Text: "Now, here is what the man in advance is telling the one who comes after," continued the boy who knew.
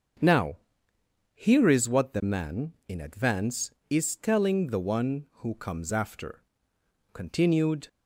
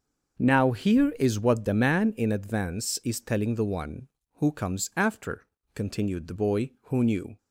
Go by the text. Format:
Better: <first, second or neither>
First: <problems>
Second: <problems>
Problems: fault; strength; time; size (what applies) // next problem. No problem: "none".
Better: second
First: starts louder than the rest; until 1.9 s; 7 dB // stops before "the boy who knew"; at 7.8 s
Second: starts louder than the rest; until 1.4 s; 6 dB